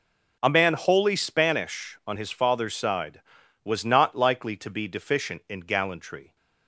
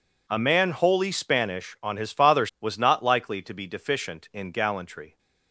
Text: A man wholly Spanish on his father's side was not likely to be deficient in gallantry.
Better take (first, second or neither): first